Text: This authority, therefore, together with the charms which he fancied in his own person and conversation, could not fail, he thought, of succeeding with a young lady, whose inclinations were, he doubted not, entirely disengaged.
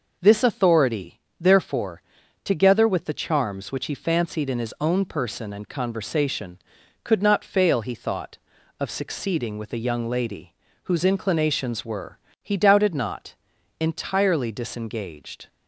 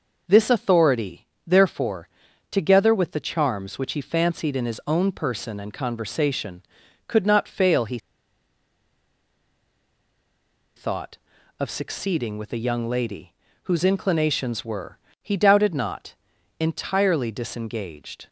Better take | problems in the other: first | pauses between "he" and "thought"; strong; at 7.9 s; 2.7 s long

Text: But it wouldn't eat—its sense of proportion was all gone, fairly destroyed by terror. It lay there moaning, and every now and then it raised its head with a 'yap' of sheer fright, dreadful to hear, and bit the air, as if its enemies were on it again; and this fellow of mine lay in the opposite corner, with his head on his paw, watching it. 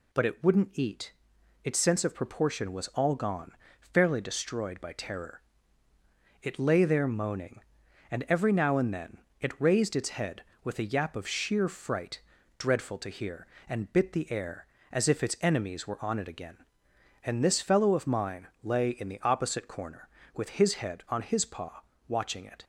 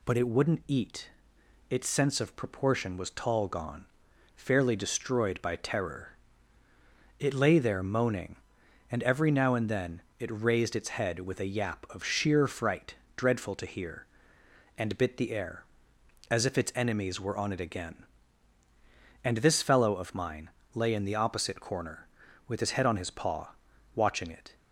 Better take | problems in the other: first | says "tall" for "all"; at 3.1 s // pauses between "then" and "it"; slight; at 10.0 s; 0.18 s long; slight in the first // pauses between "mine" and "lay"; slight; at 20.4 s; 0.26 s long; slight in the first

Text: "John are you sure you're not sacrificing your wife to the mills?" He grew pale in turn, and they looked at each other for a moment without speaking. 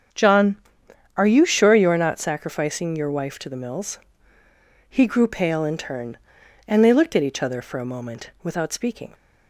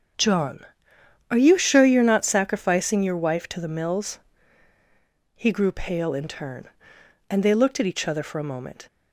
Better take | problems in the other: first | starts louder than the rest; strong; until 1.8 s; 7 dB; strong in the first // stops before "without speaking"; at 8.8 s

